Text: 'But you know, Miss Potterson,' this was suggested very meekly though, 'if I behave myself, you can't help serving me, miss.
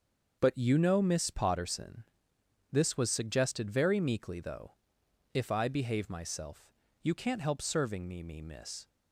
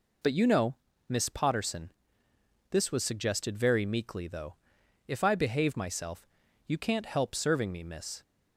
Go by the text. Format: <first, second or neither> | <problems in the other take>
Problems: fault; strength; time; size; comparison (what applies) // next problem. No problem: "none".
second | starts louder than the rest; until 1.4 s; 6.5 dB // says "me" twice; at 8.2 s